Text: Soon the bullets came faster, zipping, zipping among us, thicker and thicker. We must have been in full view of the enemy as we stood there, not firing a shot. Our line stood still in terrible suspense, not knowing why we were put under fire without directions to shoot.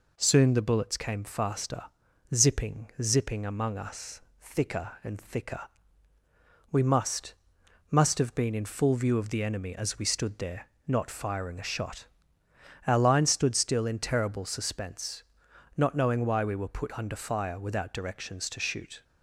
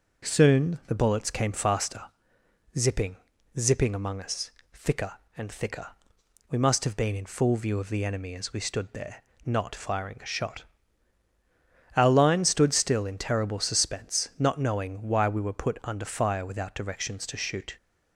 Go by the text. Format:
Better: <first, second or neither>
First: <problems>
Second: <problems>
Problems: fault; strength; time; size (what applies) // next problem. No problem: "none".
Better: second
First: says "must" twice; at 7.8 s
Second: none